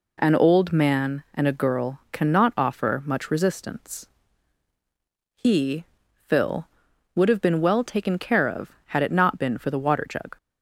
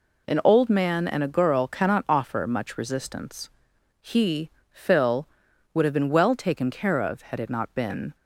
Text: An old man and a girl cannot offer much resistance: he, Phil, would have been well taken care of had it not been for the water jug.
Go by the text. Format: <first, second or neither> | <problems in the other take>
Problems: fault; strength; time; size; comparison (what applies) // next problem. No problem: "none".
first | stops before "for the water jug"; at 8.1 s